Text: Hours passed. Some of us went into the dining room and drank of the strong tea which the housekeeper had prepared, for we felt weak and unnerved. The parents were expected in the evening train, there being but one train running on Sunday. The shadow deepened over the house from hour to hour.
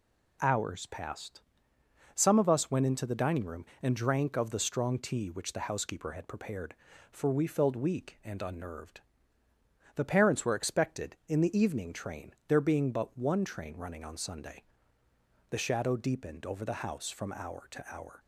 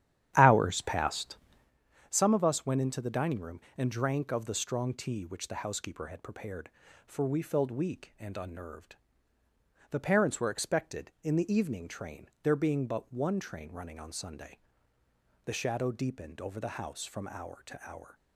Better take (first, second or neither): first